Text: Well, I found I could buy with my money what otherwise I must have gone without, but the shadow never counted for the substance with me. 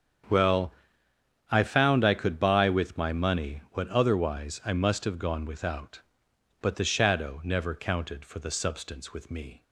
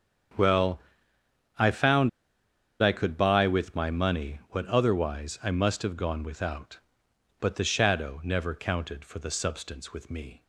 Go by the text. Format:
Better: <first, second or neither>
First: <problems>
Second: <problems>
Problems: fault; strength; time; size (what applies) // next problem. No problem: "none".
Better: first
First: starts louder than the rest; strong; until 2.0 s; 8 dB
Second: starts louder than the rest; strong; until 2.8 s; 8 dB // pauses between "found" and "I"; noticeable; at 2.0 s; 0.70 s long